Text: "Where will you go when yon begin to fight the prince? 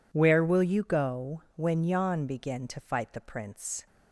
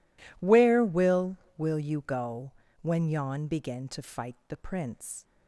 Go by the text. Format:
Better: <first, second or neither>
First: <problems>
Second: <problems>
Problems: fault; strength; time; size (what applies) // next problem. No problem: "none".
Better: first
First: pauses between "go" and "when"; slight; at 1.3 s; 0.16 s long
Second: says "will" twice; at 1.5 s // pauses between "go" and "when"; slight; at 2.5 s; 0.30 s long